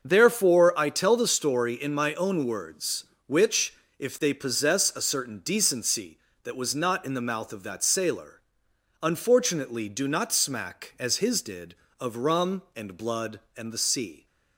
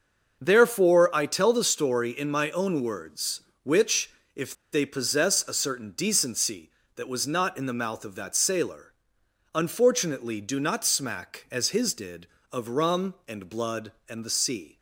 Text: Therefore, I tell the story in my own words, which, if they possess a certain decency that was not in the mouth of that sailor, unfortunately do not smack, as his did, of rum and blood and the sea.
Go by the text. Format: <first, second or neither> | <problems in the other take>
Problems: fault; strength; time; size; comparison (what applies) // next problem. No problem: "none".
first | starts louder than the rest; noticeable; until 1.4 s; 6 dB; noticeable in the first // pauses between "if" and "they"; slight; at 4.5 s; 0.18 s long